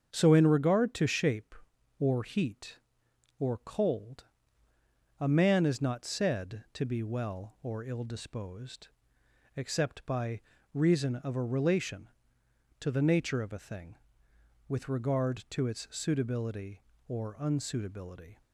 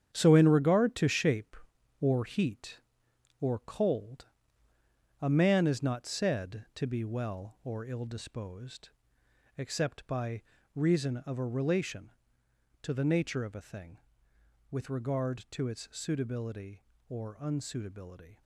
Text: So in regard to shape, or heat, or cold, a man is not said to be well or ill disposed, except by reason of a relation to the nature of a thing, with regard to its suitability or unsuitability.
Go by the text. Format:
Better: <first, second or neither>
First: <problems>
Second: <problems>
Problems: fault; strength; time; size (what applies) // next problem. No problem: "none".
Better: first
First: starts louder than the rest; strong; until 1.1 s; 7.5 dB // pauses between "by" and "reason"; slight; at 10.4 s; 0.32 s long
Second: gets quieter; strong; throughout; 9.5 dB // starts louder than the rest; strong; until 1.1 s; 9 dB // pauses between "by" and "reason"; slight; at 10.4 s; 0.32 s long